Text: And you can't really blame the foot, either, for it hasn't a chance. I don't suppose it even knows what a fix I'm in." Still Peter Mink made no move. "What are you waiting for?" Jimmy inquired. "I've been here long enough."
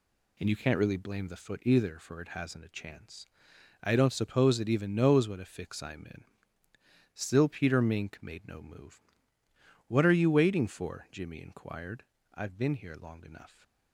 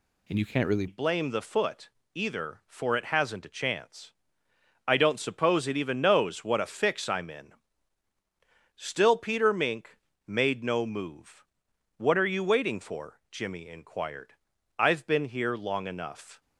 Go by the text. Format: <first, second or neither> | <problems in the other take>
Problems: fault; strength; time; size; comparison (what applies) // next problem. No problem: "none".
first | changes voice at "blame"; from 0.8 s on; 15.6 s long // pauses between "Mink" and "made"; slight; at 9.9 s; 0.30 s long